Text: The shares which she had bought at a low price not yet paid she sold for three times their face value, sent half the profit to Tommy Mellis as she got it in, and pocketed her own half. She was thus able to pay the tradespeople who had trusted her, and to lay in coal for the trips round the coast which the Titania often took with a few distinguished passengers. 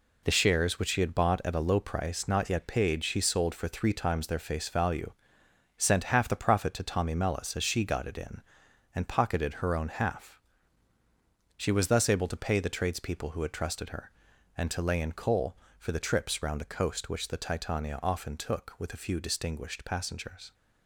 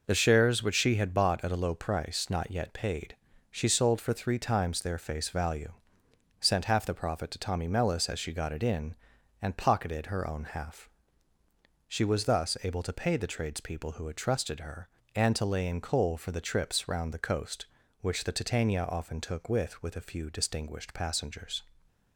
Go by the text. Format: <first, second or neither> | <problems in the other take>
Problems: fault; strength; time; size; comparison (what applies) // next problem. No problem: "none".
first | pauses between "paid" and "she"; slight; at 3.1 s; 0.34 s long // says "with" twice; at 19.8 s